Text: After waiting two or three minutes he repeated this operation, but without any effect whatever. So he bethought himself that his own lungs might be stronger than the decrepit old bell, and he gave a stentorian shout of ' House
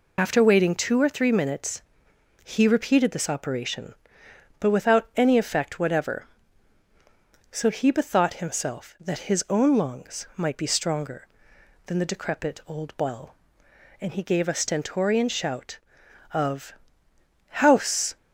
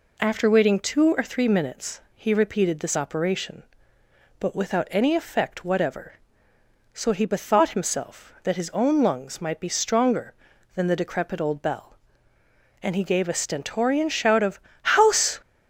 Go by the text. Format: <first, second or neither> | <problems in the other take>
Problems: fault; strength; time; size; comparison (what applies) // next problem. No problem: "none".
second | loses the start of "After"; at 0.1 s; 55 ms // pauses between "minutes" and "he"; noticeable; at 1.8 s; 0.60 s long; slight in the second